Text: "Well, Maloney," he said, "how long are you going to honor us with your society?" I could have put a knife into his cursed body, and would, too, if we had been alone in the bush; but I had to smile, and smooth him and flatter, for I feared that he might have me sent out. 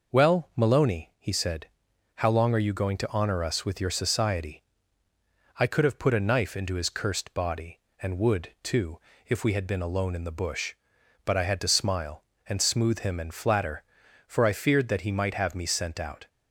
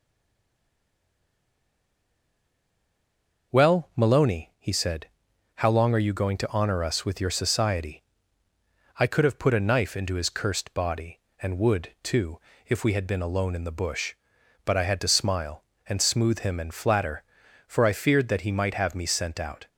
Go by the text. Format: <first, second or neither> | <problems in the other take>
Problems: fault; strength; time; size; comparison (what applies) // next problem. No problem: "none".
first | stays silent before the first word; strong; until 3.5 s; 3.5 s long